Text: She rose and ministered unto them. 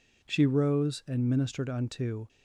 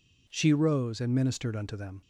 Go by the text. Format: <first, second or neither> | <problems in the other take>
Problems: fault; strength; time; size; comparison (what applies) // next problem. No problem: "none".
second | stops before "them"; at 2.2 s